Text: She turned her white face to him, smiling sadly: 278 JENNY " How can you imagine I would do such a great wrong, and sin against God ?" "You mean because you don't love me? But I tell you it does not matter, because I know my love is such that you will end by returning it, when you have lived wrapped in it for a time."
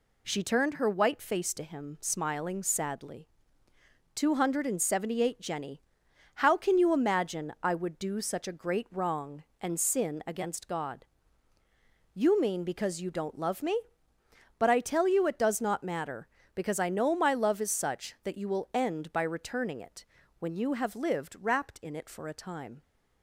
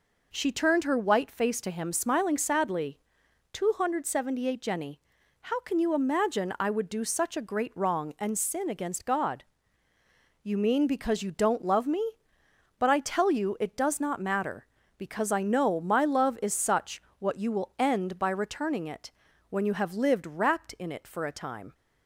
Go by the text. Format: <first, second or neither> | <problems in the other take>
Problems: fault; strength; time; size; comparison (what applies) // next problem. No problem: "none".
first | says "what" for "that"; at 17.1 s